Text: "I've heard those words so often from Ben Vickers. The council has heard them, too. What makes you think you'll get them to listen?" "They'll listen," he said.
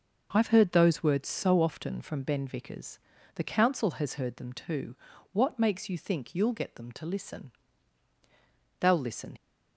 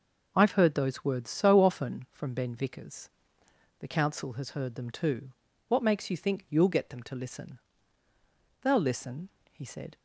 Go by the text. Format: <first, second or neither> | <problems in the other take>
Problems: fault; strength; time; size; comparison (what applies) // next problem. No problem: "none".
second | stops before "he said"; at 9.3 s